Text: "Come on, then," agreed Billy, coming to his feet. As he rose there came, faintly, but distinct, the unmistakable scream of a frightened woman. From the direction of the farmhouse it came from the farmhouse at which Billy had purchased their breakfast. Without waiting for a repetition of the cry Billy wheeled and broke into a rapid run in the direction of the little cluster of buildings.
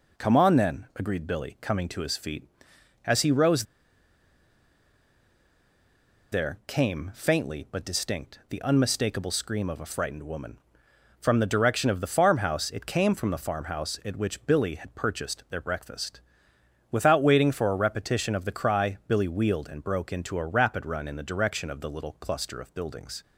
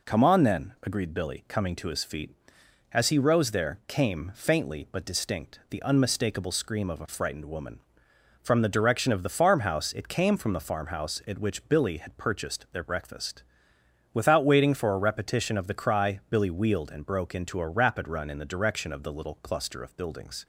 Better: second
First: pauses between "rose" and "there"; strong; at 3.6 s; 2.6 s long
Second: none

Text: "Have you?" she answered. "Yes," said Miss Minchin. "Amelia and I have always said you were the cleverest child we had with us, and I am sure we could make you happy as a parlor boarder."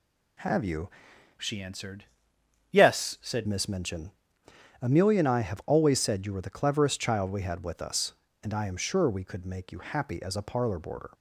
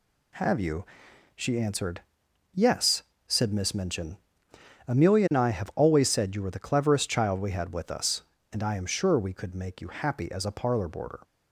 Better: second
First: changes voice from "she" to "said"; from 1.3 to 3.4 s; 2.1 s long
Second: none

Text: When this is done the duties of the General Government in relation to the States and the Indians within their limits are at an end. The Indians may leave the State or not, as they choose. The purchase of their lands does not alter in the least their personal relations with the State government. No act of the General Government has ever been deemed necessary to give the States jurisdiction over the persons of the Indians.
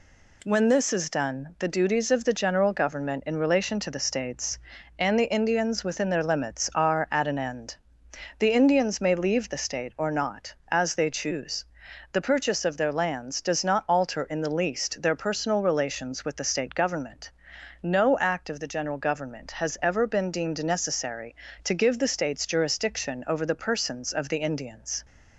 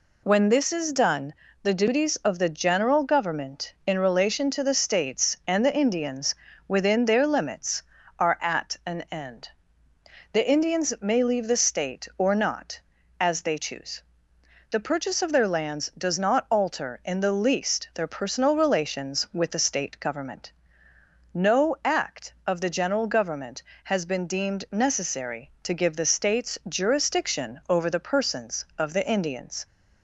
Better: first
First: none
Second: pauses between "done" and "the"; slight; at 1.3 s; 0.28 s long // pauses between "Indians" and "within"; slight; at 6.3 s; 0.32 s long // skips "ever"; at 24.0 s

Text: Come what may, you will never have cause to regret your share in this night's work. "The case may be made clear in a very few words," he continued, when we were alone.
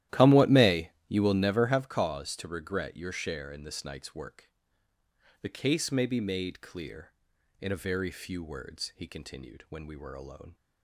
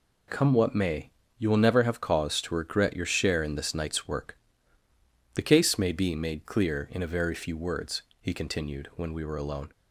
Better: second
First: starts louder than the rest; strong; until 1.8 s; 13.5 dB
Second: none

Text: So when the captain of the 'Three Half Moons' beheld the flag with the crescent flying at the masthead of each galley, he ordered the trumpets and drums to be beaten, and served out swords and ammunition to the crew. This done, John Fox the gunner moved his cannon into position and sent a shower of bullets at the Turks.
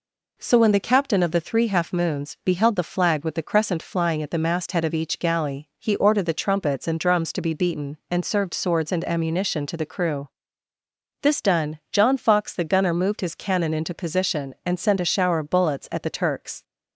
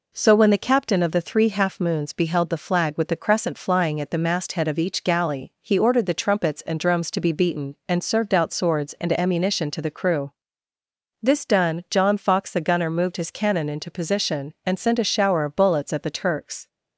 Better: second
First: skips "out"; at 8.5 s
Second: none

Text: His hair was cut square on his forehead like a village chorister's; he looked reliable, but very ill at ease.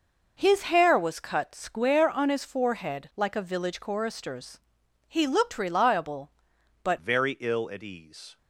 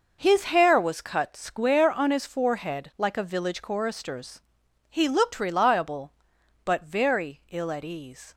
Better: second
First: changes voice at "very"; from 6.9 s on; 1.4 s long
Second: none

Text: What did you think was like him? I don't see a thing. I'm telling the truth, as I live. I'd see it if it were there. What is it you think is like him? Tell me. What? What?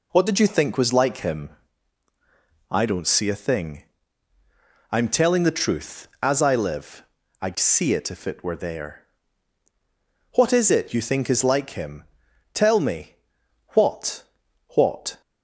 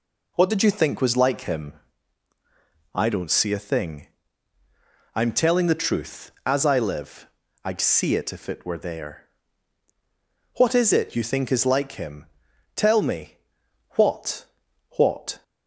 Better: neither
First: none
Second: none

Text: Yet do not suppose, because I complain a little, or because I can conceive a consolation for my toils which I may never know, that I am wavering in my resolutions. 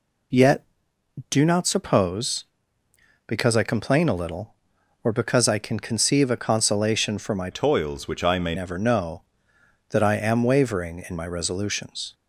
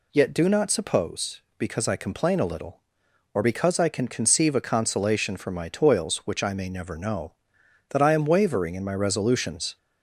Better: second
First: changes voice from "toils" to "may"; from 7.5 to 8.5 s; 1.0 s long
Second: none

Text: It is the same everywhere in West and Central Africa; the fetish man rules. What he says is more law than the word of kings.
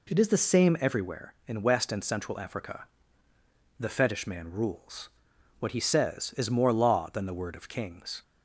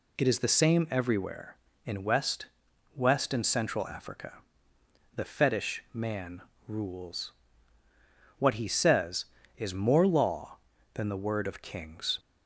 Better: first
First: none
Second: says "West" twice; at 2.9 s // pauses between "man" and "rules"; slight; at 6.4 s; 0.28 s long

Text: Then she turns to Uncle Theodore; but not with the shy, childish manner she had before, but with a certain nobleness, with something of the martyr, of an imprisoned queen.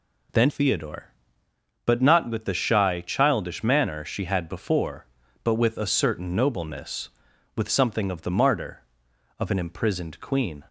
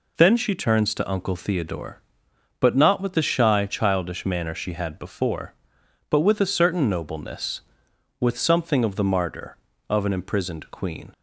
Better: second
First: skips "she turns to Uncle"; at 0.4 s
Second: none

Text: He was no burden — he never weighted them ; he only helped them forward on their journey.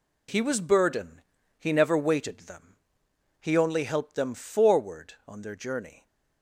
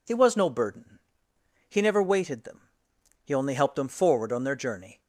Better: second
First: skips "no"; at 0.6 s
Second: none

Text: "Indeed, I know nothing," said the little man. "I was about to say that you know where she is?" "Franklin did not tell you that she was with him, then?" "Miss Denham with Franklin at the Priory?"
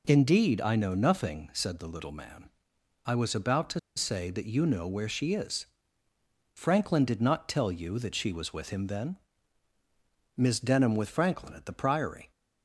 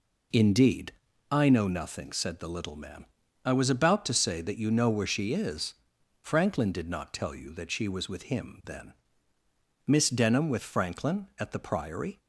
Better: second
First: pauses between "to" and "say"; slight; at 3.7 s; 0.16 s long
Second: none

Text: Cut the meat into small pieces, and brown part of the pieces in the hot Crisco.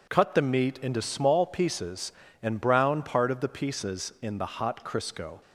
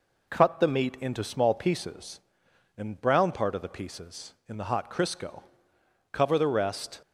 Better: first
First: none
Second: goes on to say "Cover the rest"; noticeable; from 6.1 s on; 0.90 s long

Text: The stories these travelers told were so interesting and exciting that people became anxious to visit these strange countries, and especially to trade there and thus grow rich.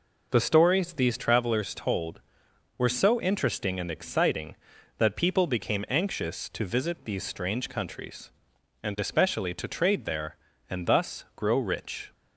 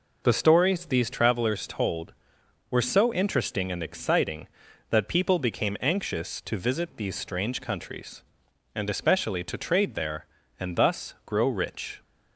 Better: neither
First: none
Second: none

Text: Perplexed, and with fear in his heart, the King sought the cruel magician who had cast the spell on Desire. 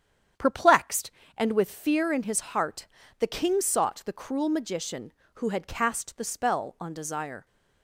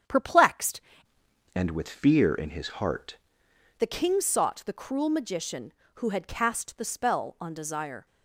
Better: first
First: starts louder than the rest; strong; until 1.6 s; 9 dB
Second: starts louder than the rest; strong; until 1.8 s; 8.5 dB // changes voice from "and" to "heart"; from 1.5 to 3.1 s; 1.6 s long

